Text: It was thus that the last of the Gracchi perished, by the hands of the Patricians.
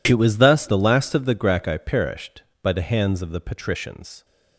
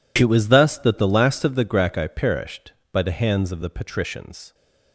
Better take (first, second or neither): second